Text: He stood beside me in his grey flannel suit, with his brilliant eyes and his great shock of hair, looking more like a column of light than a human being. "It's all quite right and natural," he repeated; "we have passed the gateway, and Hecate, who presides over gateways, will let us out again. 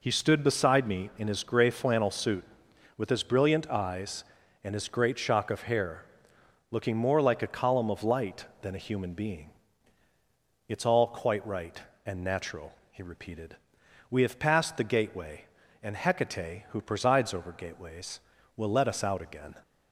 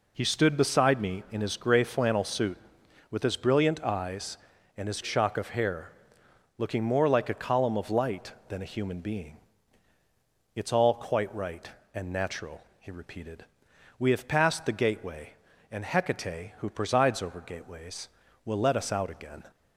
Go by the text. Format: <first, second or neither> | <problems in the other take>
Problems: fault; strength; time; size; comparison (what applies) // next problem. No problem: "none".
first | skips "great"; at 5.0 s